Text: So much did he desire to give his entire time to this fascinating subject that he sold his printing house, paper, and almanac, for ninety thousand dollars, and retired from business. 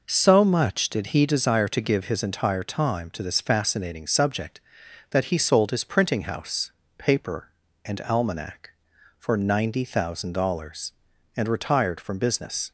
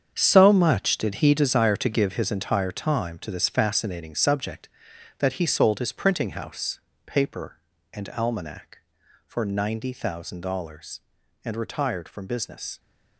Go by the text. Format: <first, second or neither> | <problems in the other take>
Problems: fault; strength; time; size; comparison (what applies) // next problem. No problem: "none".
first | gets quieter; strong; throughout; 12 dB